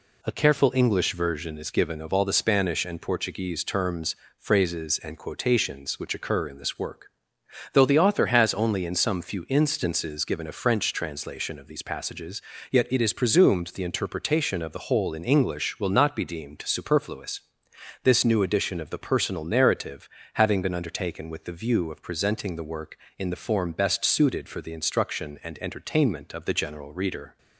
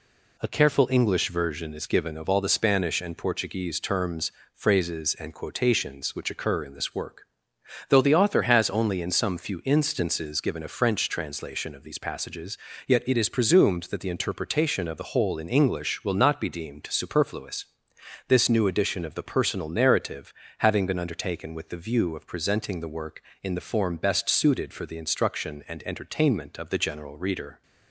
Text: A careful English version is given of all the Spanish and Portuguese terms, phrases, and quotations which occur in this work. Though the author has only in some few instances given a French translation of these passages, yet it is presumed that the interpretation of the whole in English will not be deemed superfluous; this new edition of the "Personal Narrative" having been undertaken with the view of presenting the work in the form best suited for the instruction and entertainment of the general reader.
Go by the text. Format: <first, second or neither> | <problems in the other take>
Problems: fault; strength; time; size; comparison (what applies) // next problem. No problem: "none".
second | skips "that"; at 13.7 s // pauses between "Narrative" and "having"; slight; at 20.0 s; 0.24 s long; slight in the second